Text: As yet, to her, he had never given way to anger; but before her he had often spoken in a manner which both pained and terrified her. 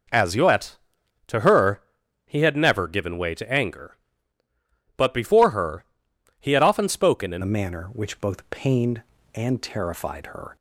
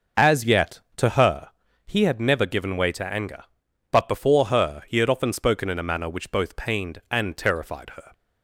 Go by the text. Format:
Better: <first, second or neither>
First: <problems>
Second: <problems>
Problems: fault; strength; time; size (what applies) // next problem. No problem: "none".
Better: second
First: pauses between "her" and "he"; noticeable; at 5.8 s; 0.56 s long // changes voice at "a"; from 7.4 s on; 3.1 s long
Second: none